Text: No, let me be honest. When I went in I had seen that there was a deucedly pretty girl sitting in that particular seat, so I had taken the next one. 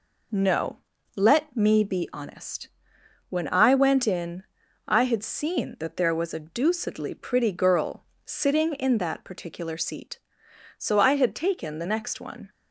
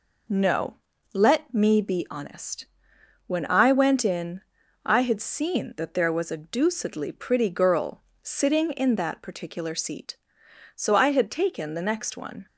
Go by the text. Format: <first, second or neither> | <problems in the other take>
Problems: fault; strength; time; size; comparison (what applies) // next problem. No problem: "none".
neither | pauses between "in" and "I"; the same in both // pauses between "girl" and "sitting"; slight; the same in both